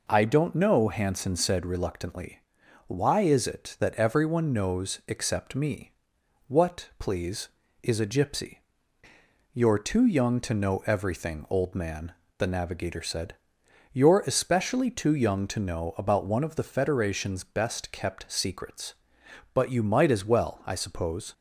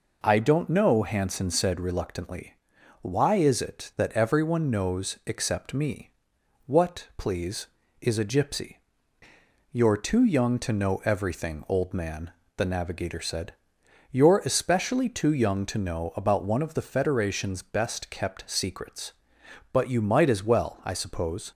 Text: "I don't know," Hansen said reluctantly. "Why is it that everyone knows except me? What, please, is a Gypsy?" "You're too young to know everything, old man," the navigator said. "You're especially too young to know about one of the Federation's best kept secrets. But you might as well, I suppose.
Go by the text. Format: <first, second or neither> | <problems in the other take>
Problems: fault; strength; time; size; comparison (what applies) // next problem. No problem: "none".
neither | none